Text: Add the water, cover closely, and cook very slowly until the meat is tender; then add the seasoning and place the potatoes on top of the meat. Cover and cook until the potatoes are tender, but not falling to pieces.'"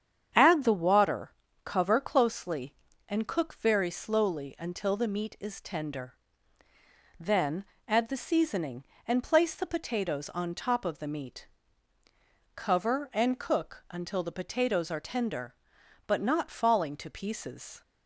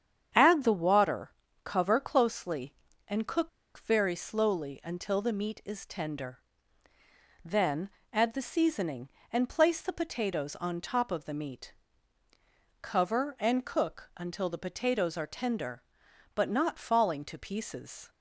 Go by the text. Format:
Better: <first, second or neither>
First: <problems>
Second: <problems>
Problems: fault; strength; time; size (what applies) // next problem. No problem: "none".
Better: first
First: starts louder than the rest; strong; until 1.6 s; 8.5 dB // pauses between "then" and "add"; slight; at 7.6 s; 0.22 s long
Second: starts louder than the rest; strong; until 1.6 s; 8.5 dB // pauses between "cook" and "very"; slight; at 3.4 s; 0.28 s long // pauses between "then" and "add"; slight; at 7.8 s; 0.22 s long